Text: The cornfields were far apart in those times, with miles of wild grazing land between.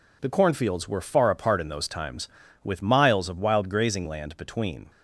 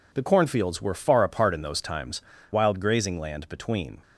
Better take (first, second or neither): first